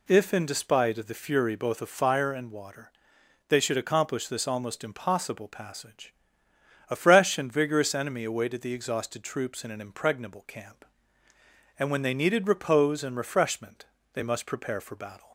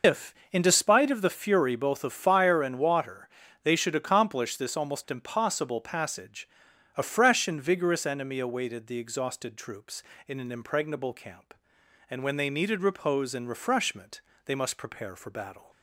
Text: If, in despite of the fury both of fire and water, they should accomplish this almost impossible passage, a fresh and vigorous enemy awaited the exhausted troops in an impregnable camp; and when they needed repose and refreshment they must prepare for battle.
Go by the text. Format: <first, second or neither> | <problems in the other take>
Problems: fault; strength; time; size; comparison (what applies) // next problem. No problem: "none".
first | loses the start of "If"; at 0.0 s; 130 ms // pauses between "refreshment" and "they"; slight; at 14.2 s; 0.26 s long; slight in the first